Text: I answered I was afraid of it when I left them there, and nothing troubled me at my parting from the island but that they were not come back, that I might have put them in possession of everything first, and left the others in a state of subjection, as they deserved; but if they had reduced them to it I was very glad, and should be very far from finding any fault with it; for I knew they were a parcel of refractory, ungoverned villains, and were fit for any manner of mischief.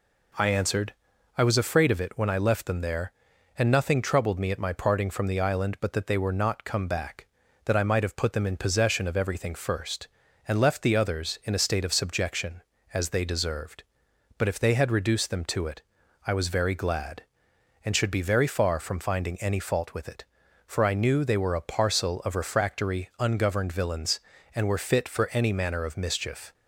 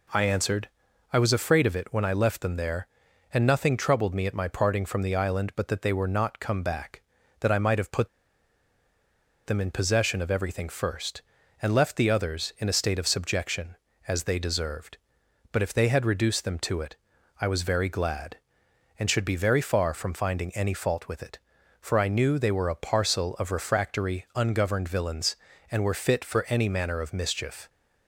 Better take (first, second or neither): first